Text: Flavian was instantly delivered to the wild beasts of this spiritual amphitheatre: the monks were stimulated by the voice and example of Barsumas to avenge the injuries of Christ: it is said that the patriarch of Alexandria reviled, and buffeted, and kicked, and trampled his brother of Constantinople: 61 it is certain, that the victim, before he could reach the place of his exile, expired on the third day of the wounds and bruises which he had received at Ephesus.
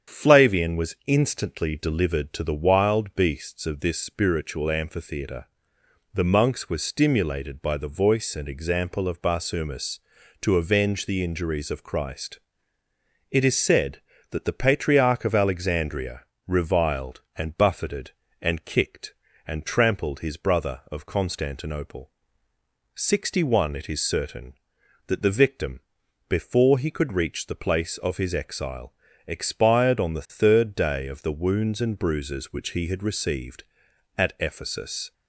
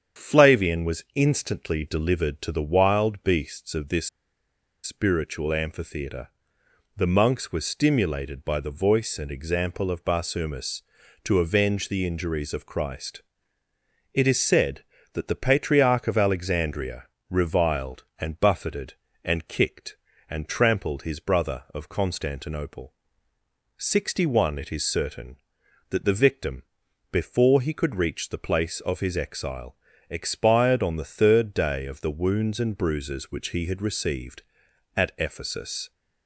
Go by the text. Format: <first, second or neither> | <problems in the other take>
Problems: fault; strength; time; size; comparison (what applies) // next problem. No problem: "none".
first | starts louder than the rest; strong; until 1.2 s; 8 dB; strong in the first // pauses between "this" and "spiritual"; noticeable; at 4.0 s; 0.74 s long // pauses between "Alexandria" and "reviled"; slight; at 17.0 s; 0.24 s long; slight in the first